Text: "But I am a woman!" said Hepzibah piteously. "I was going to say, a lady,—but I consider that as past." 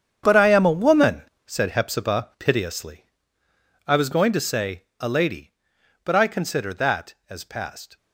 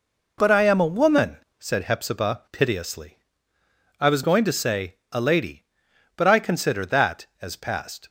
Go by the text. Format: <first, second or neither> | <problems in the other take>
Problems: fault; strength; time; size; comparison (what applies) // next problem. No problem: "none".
second | gets quieter; strong; throughout; 13.5 dB